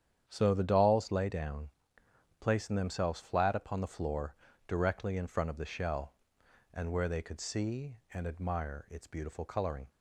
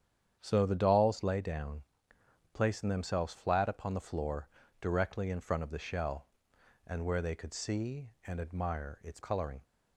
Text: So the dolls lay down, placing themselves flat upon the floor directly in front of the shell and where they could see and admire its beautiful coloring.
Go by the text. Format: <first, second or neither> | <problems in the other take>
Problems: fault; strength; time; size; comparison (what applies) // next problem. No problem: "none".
first | starts louder than the rest; strong; until 1.4 s; 8.5 dB; strong in the first // pauses between "floor" and "directly"; slight; at 4.4 s; 0.32 s long; slight in the first // skips "beautiful"; at 9.2 s